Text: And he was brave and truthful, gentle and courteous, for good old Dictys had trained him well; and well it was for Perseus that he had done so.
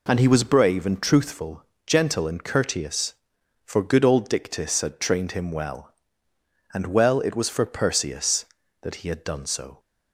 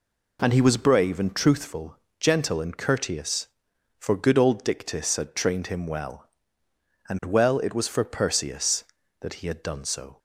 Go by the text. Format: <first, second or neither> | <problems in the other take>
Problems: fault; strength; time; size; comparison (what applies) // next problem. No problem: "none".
neither | none